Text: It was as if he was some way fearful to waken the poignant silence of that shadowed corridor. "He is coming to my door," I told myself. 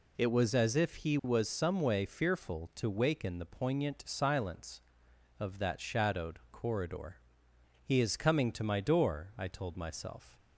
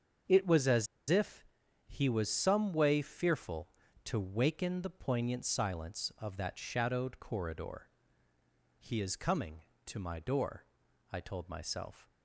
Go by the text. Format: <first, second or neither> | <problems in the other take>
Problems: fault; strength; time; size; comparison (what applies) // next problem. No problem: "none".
first | starts louder than the rest; until 1.9 s; 6.5 dB // pauses between "as" and "if"; slight; at 0.8 s; 0.22 s long // pauses between "if" and "he"; at 1.4 s; 0.42 s long